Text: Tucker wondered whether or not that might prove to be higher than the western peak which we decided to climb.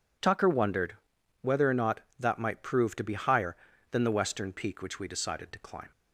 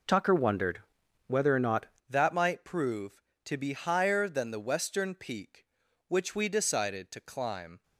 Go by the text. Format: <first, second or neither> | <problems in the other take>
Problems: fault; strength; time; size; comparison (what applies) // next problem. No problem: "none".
first | pauses between "wondered" and "whether"; noticeable; at 0.7 s; 0.48 s long; noticeable in the first // changes voice at "that"; from 2.0 s on; 5.8 s long